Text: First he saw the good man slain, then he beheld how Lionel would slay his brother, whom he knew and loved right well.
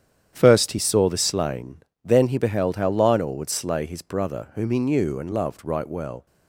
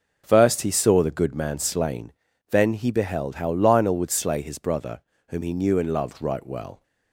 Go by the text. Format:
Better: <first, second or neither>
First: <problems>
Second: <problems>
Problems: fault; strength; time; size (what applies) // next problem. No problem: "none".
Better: second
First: starts louder than the rest; strong; until 1.3 s; 9 dB // skips "good man"; at 1.1 s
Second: none